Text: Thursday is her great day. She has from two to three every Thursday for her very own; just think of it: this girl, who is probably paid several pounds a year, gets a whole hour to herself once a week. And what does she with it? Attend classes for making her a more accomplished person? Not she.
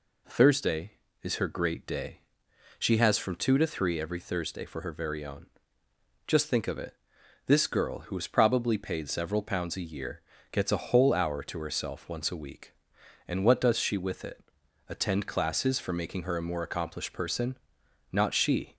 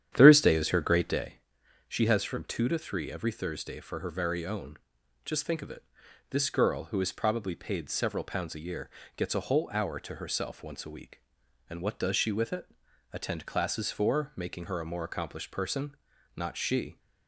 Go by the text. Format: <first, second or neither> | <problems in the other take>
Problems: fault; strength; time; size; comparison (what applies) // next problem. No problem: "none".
first | starts louder than the rest; strong; until 1.3 s; 10 dB